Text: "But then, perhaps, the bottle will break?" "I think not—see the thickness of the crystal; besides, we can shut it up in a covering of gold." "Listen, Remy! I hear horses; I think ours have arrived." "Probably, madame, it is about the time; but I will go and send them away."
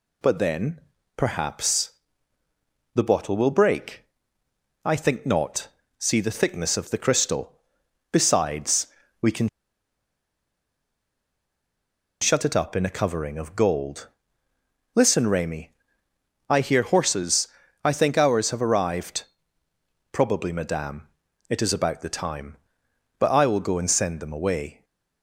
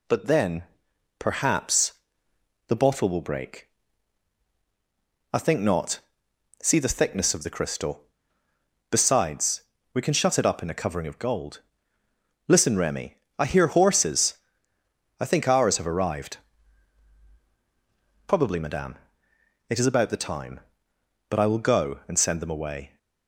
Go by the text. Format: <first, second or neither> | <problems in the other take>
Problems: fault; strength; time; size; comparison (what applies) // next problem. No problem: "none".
second | pauses between "can" and "shut"; strong; at 9.4 s; 2.7 s long